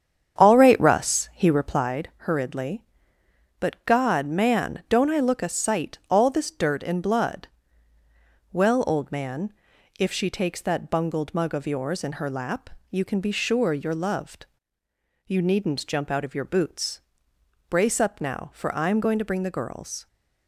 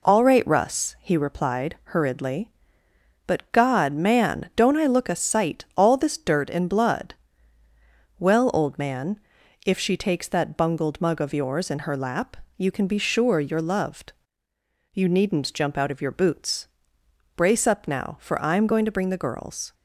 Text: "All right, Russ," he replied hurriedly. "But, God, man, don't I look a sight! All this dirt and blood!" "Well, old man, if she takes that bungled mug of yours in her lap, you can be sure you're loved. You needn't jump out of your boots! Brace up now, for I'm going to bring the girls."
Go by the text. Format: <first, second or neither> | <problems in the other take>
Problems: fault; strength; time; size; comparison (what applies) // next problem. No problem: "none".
second | starts louder than the rest; strong; until 2.0 s; 8 dB